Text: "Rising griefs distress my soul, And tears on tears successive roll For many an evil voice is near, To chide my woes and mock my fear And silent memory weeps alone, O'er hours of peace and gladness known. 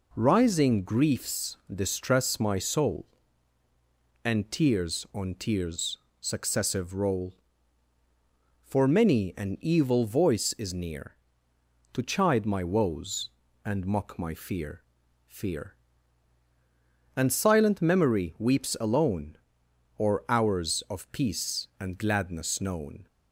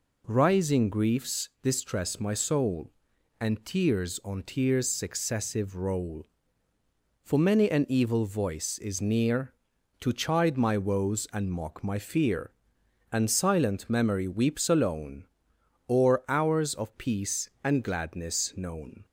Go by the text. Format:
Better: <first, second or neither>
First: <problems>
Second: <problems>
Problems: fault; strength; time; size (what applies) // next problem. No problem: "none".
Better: second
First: pauses between "griefs" and "distress"; slight; at 1.5 s; 0.18 s long // pauses between "tears" and "successive"; slight; at 5.9 s; 0.24 s long // says "fear" twice; at 15.2 s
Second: none